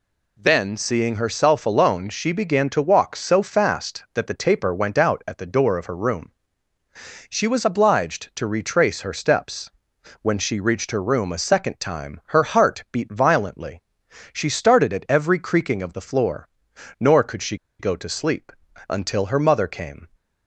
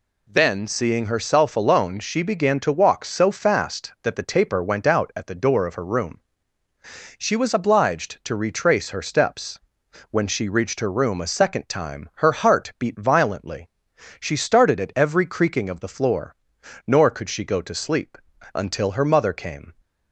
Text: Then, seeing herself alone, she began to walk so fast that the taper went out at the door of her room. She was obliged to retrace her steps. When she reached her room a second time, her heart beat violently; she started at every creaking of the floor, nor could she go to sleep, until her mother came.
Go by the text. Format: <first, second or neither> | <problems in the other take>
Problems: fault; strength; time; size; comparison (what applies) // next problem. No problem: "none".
second | pauses between "she" and "go"; slight; at 17.5 s; 0.23 s long